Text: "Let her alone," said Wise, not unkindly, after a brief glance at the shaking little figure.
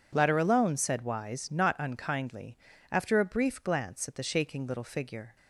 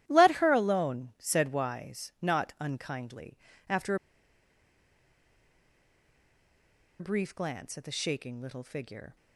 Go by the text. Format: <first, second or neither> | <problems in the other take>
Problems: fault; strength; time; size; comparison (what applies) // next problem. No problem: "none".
first | starts louder than the rest; strong; until 1.0 s; 12.5 dB // pauses between "after" and "a"; strong; at 3.9 s; 3.0 s long